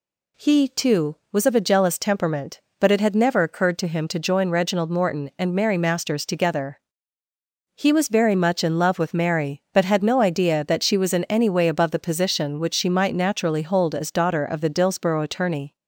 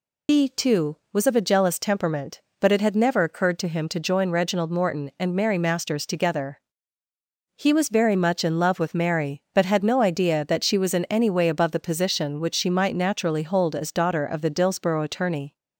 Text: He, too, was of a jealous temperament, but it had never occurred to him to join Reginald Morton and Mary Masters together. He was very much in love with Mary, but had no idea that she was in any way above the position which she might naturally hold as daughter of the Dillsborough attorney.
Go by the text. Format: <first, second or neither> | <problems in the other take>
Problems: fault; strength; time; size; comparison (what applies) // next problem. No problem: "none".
first | loses the start of "He"; at 0.2 s; 130 ms